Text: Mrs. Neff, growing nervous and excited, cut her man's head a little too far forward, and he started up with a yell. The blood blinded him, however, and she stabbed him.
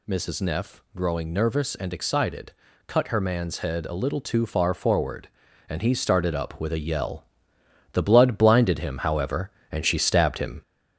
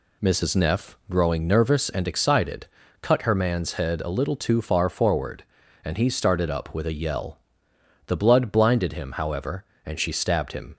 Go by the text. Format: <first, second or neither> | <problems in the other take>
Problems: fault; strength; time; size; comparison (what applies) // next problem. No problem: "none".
second | gets louder; slight; throughout; 3.5 dB